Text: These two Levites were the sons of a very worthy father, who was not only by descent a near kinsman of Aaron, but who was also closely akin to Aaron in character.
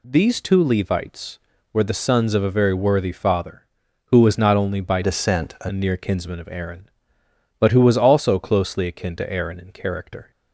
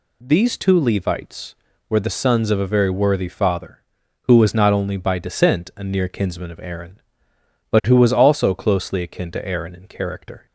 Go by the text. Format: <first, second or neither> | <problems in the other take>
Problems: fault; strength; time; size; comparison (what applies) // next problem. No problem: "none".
second | changes voice from "descent" to "a"; from 5.0 to 5.6 s; 0.6 s long